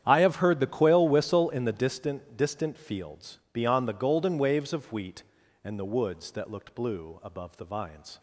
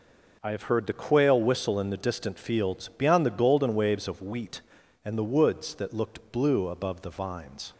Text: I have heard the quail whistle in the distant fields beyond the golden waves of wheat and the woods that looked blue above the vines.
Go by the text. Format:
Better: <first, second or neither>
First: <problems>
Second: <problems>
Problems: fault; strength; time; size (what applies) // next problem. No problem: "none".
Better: second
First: starts louder than the rest; strong; until 1.0 s; 10 dB // says "distant" twice; at 2.3 s // pauses between "fields" and "beyond"; slight; at 3.3 s; 0.16 s long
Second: none